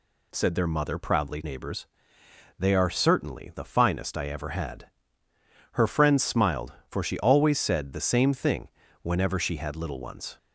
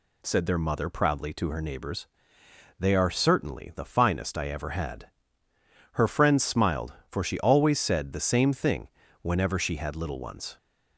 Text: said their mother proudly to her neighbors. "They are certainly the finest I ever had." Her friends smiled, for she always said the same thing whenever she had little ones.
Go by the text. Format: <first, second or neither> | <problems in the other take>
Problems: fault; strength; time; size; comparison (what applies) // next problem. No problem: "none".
second | skips "to her"; at 1.4 s // pauses between "thing" and "whenever"; slight; at 8.6 s; 0.36 s long; slight in the second